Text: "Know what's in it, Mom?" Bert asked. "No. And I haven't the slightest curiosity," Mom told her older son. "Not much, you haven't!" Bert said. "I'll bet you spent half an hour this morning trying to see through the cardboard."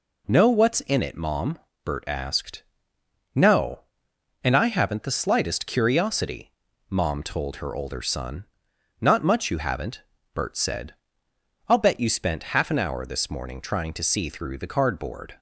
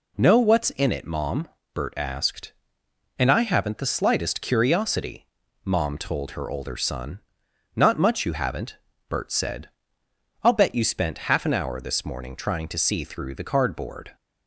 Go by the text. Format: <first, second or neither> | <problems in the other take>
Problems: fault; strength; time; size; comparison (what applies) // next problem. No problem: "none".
first | skips "No"; at 2.8 s